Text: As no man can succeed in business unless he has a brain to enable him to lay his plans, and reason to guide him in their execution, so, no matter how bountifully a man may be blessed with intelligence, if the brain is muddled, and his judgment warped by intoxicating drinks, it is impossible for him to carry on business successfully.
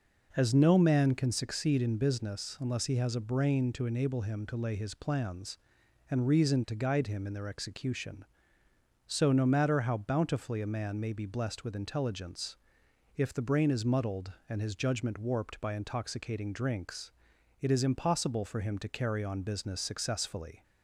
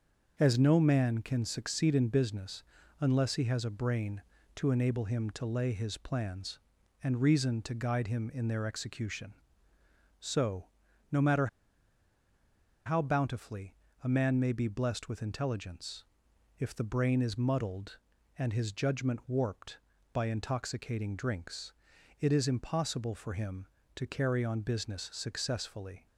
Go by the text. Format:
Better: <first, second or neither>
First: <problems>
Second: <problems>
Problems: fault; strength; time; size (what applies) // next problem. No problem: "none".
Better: first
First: none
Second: starts louder than the rest; noticeable; until 1.4 s; 6 dB // pauses between "business" and "unless"; slight; at 2.6 s; 0.36 s long // pauses between "matter" and "how"; strong; at 11.4 s; 1.3 s long // pauses between "bountifully" and "a"; slight; at 13.7 s; 0.28 s long